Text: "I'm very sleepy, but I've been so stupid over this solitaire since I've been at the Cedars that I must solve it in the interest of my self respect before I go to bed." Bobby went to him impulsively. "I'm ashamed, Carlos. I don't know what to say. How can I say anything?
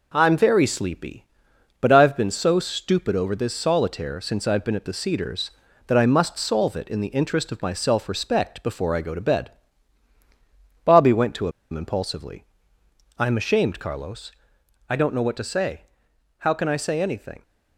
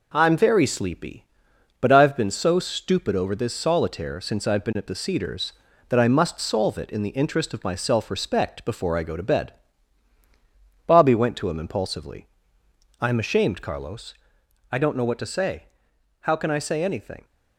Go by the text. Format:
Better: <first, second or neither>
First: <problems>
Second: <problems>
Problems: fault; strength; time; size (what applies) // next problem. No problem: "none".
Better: second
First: pauses between "to" and "him"; slight; at 11.4 s; 0.22 s long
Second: none